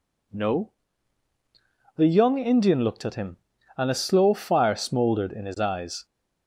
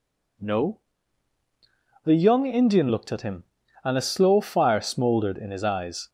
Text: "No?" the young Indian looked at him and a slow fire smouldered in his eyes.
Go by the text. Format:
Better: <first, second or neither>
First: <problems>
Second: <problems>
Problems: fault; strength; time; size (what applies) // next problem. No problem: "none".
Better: neither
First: none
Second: none